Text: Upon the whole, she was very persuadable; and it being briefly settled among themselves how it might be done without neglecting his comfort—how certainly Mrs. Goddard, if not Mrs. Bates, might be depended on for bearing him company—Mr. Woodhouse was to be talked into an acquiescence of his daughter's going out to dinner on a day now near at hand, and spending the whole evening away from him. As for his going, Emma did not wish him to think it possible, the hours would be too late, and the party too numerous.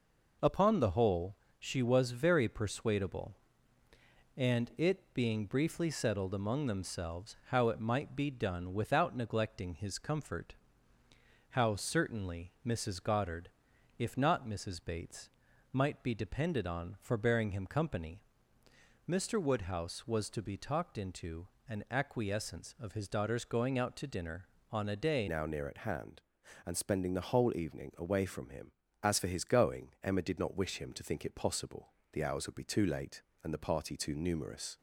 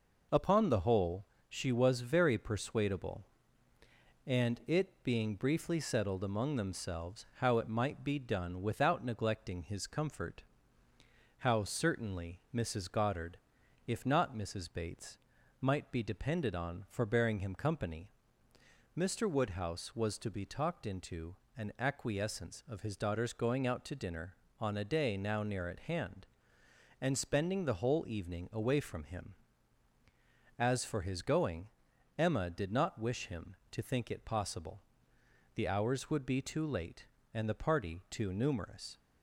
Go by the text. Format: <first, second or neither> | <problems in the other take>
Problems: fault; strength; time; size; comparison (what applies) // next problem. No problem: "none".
second | pauses between "into" and "an"; slight; at 21.4 s; 0.22 s long; slight in the second // changes voice at "now"; from 25.2 s on; 9.5 s long